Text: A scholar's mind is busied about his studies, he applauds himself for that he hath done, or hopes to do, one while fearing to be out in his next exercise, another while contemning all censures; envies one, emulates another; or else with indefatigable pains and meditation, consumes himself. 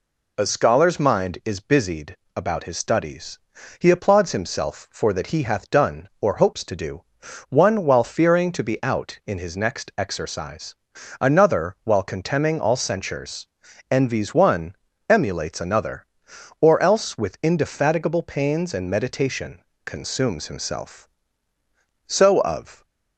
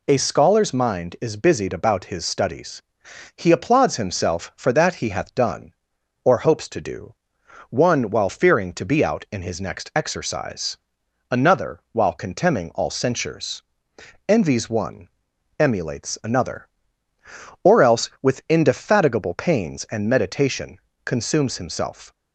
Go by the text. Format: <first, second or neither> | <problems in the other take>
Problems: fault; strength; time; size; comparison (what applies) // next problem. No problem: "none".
second | pauses between "busied" and "about"; slight; at 2.1 s; 0.20 s long // goes on to say "So of"; noticeable; from 22.0 s on; 0.78 s long